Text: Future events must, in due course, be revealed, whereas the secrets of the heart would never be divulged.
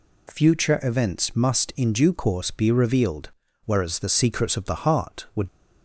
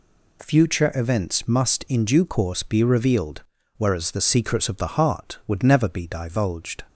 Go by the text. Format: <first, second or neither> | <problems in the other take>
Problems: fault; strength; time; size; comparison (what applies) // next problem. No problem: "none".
second | stops before "never be divulged"; at 5.4 s